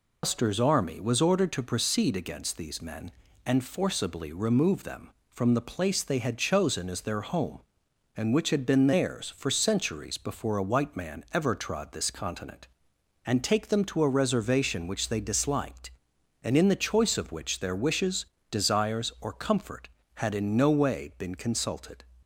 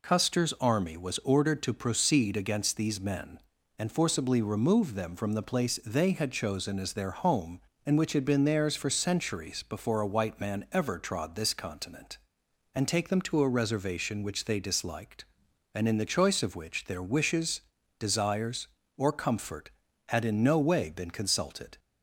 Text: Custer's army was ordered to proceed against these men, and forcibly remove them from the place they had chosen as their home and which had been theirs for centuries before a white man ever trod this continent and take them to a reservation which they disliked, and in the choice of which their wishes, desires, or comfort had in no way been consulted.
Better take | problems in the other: second | loses the start of "Custer's"; at 0.2 s; 145 ms

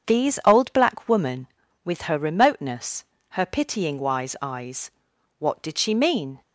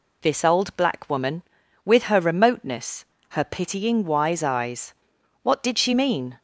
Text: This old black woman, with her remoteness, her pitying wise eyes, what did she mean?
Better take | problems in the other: second | starts louder than the rest; strong; until 1.1 s; 7.5 dB // says "These" for "This"; at 0.0 s

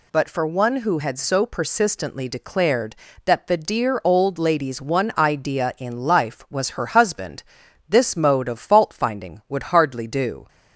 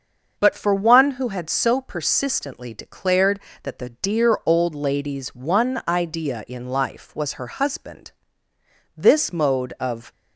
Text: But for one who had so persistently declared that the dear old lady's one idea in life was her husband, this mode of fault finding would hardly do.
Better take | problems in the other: first | starts louder than the rest; until 1.3 s; 6.5 dB // stops before "fault finding would hardly do"; at 10.1 s

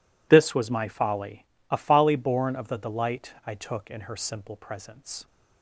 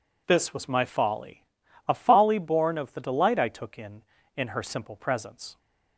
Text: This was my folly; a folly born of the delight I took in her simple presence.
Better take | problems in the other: first | says "in" twice; at 4.3 s

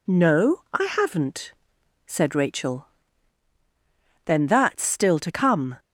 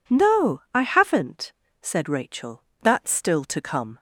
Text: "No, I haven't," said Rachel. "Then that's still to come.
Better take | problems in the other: first | skips "Then"; at 2.7 s

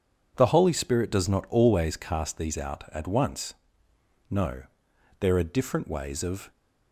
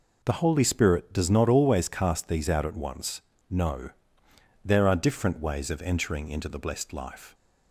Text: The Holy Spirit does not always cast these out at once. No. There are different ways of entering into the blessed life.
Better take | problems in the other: second | stops before "entering into the blessed life"; at 6.5 s

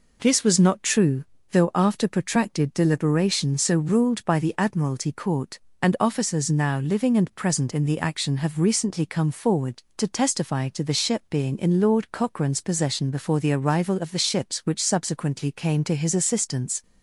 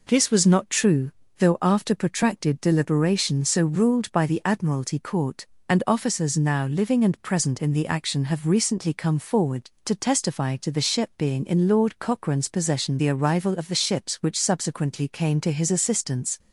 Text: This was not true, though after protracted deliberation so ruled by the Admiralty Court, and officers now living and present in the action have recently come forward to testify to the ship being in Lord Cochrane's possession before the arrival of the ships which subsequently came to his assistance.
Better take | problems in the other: first | skips "before"; at 12.9 s

